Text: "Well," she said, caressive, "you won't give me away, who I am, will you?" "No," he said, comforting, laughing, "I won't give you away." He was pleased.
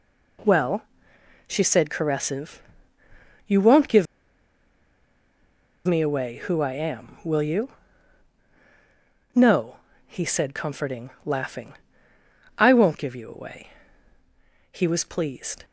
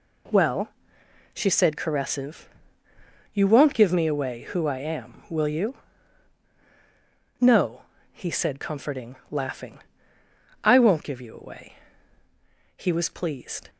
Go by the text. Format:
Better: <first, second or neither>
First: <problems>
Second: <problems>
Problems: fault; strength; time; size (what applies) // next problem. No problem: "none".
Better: second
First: pauses between "give" and "me"; strong; at 4.0 s; 1.8 s long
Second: none